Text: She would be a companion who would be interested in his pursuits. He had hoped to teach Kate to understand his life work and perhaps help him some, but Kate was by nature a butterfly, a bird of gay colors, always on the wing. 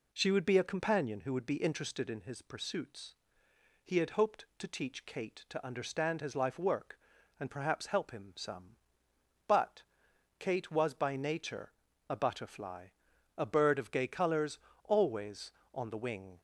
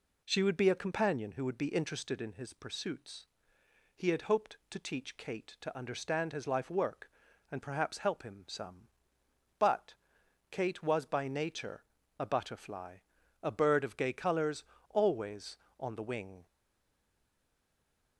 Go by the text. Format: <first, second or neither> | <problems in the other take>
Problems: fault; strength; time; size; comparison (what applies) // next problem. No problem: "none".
first | pauses between "but" and "Kate"; noticeable; at 9.9 s; 0.56 s long; noticeable in the first // pauses between "nature" and "a"; at 11.8 s; 0.36 s long; also in the first // stays silent after the last word; noticeable; from 16.4 s on; 1.7 s long